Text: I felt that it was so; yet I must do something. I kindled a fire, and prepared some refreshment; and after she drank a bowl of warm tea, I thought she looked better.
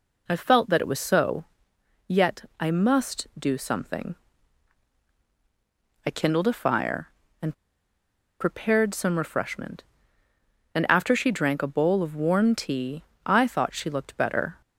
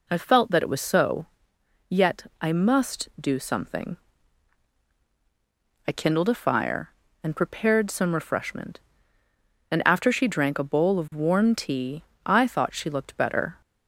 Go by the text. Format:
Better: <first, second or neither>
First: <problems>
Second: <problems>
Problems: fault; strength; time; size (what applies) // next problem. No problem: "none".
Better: second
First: pauses between "and" and "prepared"; noticeable; at 7.5 s; 0.86 s long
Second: none